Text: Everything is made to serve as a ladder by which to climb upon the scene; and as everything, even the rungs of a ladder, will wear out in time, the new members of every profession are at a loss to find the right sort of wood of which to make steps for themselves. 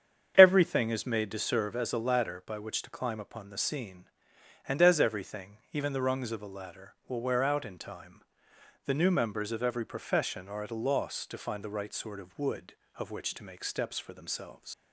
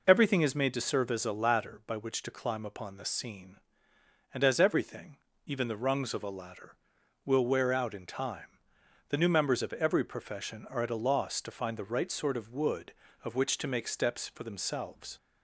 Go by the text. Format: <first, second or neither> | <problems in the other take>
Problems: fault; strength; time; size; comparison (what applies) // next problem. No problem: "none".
second | starts louder than the rest; strong; until 1.3 s; 8.5 dB // leaves "themselves" unfinished; at 14.7 s; 100 ms